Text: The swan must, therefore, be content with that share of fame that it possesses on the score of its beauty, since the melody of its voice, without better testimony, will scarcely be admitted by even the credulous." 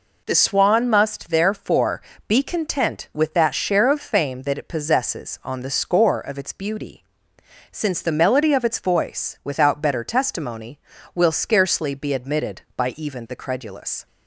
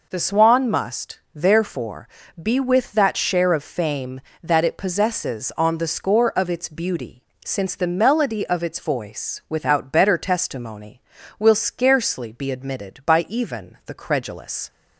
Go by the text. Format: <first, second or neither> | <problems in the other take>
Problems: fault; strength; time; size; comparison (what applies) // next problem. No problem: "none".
first | skips "content"; at 2.6 s